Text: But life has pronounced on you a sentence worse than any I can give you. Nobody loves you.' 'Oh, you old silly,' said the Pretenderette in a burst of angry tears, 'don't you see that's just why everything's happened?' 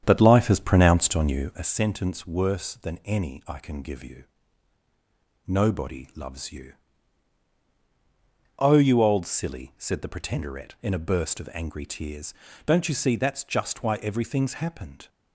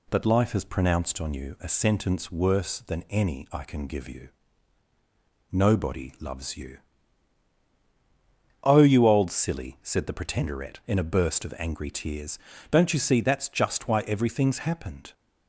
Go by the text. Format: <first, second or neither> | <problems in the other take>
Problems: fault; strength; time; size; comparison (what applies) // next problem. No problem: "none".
second | starts louder than the rest; strong; until 1.7 s; 8.5 dB